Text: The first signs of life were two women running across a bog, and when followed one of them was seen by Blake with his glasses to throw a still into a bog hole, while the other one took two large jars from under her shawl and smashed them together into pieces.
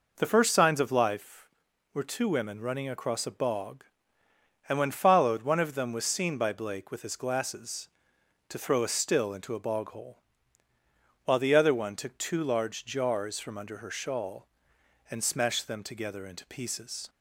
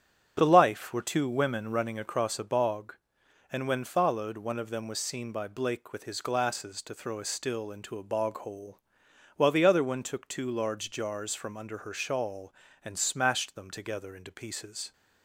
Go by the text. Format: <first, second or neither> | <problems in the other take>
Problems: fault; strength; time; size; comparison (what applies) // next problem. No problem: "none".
first | starts louder than the rest; strong; until 1.3 s; 8 dB // skips "first signs of"; at 0.4 s